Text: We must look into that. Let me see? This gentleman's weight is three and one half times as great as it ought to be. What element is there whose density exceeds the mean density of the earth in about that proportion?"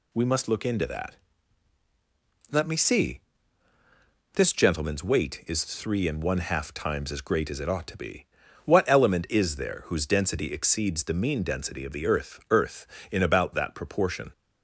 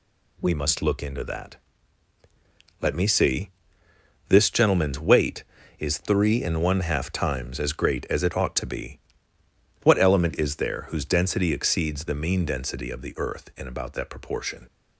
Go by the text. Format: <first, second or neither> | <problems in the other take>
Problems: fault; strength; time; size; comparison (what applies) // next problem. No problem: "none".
second | says "earth" twice; at 12.4 s